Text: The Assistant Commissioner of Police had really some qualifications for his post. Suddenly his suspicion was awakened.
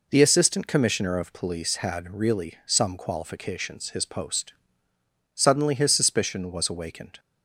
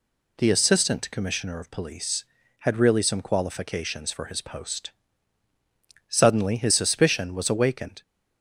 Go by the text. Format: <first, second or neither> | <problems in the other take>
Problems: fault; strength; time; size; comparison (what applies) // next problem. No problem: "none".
second | skips "for"; at 3.8 s